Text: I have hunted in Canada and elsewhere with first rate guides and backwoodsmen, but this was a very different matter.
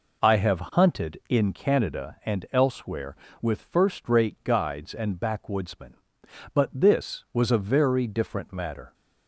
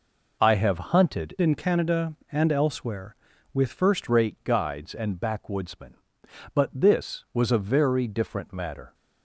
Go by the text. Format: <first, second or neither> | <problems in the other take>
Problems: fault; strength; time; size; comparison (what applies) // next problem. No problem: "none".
first | changes voice from "in" to "first"; from 1.3 to 4.0 s; 2.7 s long